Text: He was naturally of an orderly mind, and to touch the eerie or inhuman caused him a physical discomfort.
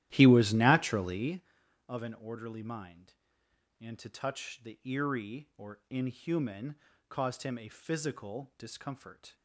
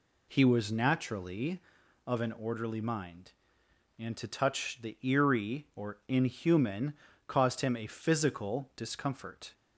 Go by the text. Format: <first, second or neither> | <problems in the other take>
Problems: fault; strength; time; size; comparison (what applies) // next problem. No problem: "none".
second | starts louder than the rest; strong; until 1.4 s; 13 dB // pauses between "inhuman" and "caused"; slight; at 6.7 s; 0.32 s long; slight in the second